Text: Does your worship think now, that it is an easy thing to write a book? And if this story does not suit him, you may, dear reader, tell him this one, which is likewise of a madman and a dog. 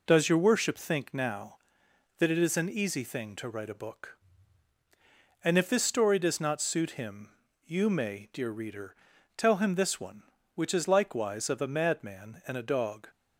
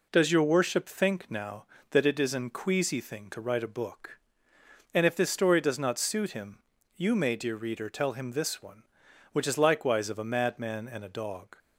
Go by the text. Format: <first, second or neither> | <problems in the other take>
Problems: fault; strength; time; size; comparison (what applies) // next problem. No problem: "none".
first | says "queasy" for "easy"; at 2.4 s